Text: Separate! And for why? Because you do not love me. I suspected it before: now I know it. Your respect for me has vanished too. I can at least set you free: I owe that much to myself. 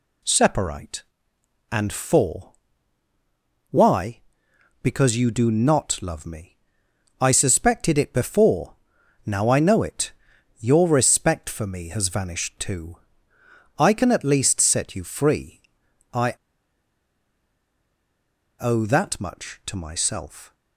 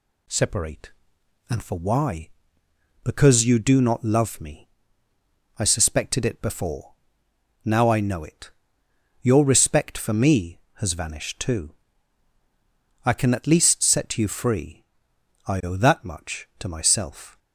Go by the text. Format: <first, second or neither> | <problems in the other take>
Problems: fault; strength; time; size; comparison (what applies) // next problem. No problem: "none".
second | pauses between "for" and "why"; at 2.5 s; 1.2 s long // pauses between "I" and "owe"; strong; at 16.3 s; 2.2 s long